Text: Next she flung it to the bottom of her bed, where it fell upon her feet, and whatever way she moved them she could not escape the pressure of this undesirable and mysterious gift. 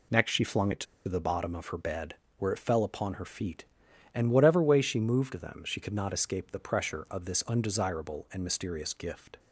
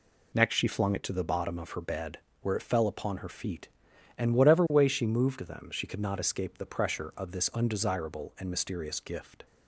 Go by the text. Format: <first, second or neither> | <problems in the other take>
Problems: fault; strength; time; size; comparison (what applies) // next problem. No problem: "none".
second | pauses between "to" and "the"; slight; at 0.8 s; 0.23 s long